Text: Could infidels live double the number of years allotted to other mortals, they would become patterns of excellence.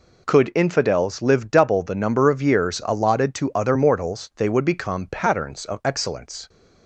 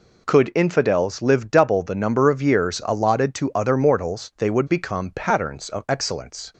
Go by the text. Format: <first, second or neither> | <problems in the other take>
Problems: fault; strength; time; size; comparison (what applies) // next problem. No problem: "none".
neither | none